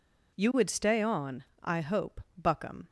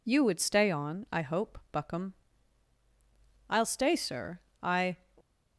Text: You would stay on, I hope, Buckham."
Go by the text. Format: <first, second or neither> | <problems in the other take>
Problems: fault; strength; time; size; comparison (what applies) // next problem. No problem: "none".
first | goes on to say "I'll stay sir I"; from 3.4 s on; 1.4 s long